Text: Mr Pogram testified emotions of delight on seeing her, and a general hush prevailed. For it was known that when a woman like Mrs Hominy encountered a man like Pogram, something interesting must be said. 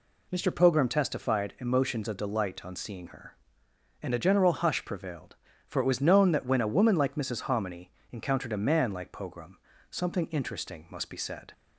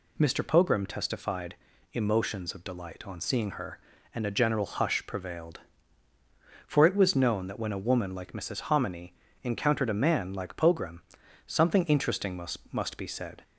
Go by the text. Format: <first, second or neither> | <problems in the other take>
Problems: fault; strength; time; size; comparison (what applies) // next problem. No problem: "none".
first | pauses between "testified" and "emotions"; at 1.5 s; 0.38 s long // pauses between "Hominy" and "encountered"; slight; at 9.1 s; 0.30 s long; slight in the first // says "must" twice; at 12.7 s